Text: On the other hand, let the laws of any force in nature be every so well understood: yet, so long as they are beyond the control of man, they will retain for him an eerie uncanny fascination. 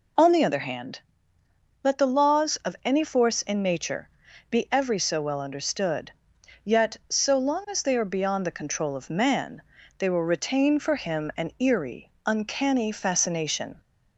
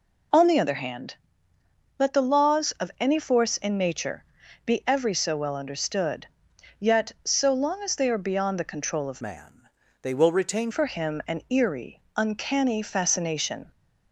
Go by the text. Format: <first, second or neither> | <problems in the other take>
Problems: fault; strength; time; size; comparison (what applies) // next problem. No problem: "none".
first | pauses between "nature" and "be"; at 4.2 s; 0.42 s long; also in the first // changes voice from "man" to "retain"; from 9.1 to 10.6 s; 1.5 s long // pauses between "eerie" and "uncanny"; slight; at 12.0 s; 0.16 s long; slight in the first